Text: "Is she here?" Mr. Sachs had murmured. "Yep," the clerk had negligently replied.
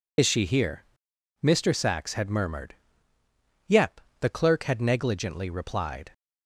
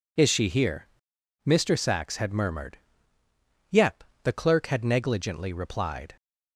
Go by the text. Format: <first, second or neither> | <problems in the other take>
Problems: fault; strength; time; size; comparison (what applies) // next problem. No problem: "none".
second | loses the start of "Is"; at 0.1 s; 35 ms